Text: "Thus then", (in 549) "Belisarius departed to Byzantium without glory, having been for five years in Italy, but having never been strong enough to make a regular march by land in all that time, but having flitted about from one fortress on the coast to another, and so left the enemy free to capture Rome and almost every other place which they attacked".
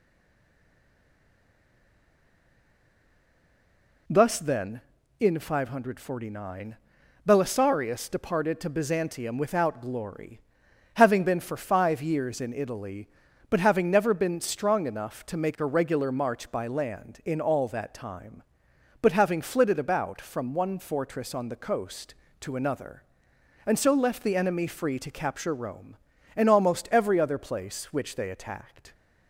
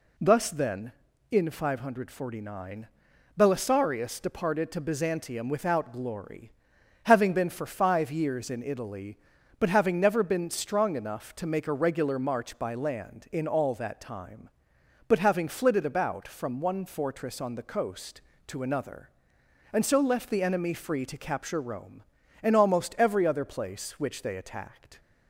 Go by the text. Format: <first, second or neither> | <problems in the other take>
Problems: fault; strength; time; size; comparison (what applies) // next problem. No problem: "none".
second | stays silent before the first word; strong; until 4.0 s; 4.0 s long